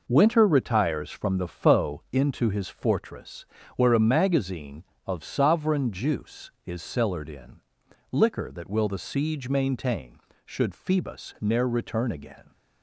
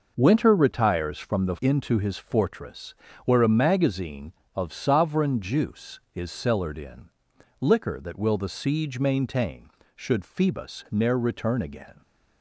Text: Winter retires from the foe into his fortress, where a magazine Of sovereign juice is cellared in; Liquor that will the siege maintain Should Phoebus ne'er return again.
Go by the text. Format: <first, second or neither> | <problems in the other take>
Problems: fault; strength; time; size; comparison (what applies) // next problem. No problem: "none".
first | skips "foe"; at 1.5 s